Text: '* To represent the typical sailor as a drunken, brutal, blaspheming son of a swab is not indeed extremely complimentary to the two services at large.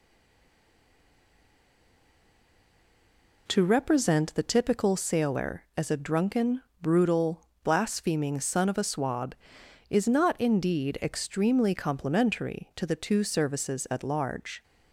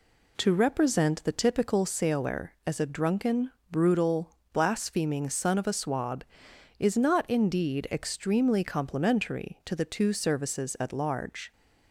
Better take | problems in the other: second | stays silent before the first word; strong; until 3.4 s; 3.4 s long

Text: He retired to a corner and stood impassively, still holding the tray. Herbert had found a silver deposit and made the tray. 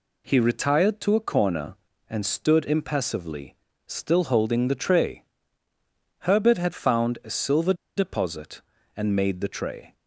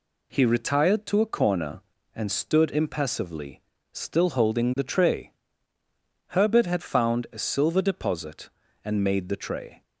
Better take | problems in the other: second | pauses between "silver" and "deposit"; slight; at 7.7 s; 0.23 s long

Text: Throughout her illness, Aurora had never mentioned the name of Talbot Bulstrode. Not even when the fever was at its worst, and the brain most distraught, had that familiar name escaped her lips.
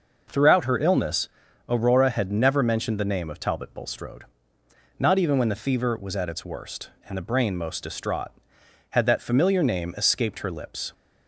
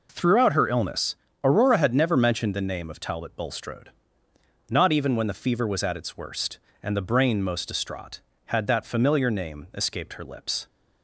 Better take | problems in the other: neither | none

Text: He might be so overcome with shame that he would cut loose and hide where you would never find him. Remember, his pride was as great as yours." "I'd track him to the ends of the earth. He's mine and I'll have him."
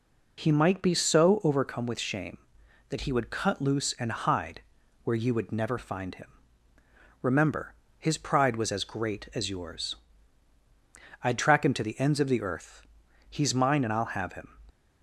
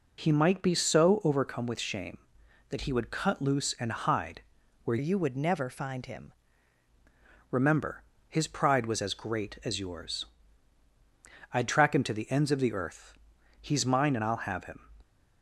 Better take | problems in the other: first | pauses between "hide" and "where"; at 4.4 s; 0.42 s long; also in the first // changes voice from "you" to "him"; from 4.9 to 6.3 s; 1.4 s long

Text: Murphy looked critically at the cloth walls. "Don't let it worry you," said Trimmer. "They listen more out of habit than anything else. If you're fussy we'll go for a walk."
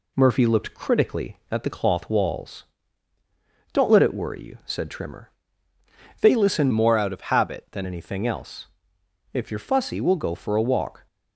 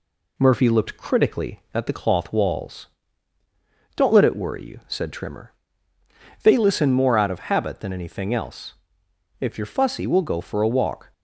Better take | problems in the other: second | changes voice from "more" to "than"; from 6.7 to 7.8 s; 1.1 s long

